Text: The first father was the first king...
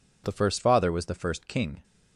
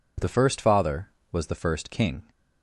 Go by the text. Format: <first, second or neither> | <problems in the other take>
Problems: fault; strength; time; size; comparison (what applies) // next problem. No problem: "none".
neither | none